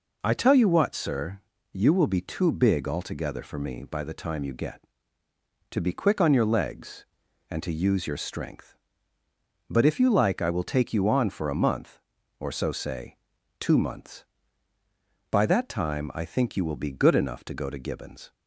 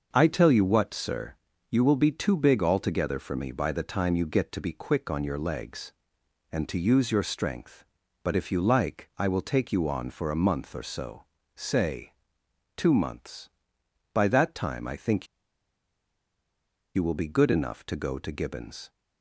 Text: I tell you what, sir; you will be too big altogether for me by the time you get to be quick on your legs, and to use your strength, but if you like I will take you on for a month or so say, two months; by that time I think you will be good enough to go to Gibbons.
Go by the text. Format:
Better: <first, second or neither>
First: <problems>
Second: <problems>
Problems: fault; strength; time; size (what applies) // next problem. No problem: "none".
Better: first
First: none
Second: starts louder than the rest; until 1.1 s; 6 dB // pauses between "so" and "say"; slight; at 11.2 s; 0.30 s long // pauses between "think" and "you"; strong; at 15.2 s; 1.6 s long